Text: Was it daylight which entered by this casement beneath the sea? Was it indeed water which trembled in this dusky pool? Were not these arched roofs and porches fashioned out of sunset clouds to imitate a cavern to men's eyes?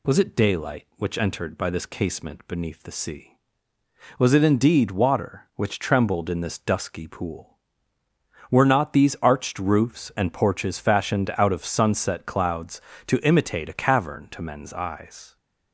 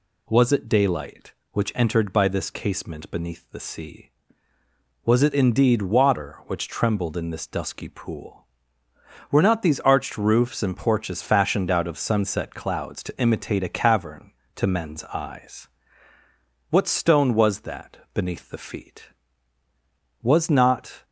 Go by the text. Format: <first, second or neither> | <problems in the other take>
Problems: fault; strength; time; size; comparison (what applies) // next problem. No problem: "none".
first | goes on to say "What stone was that beneath the feet Was not"; strong; from 16.7 s on; 4.3 s long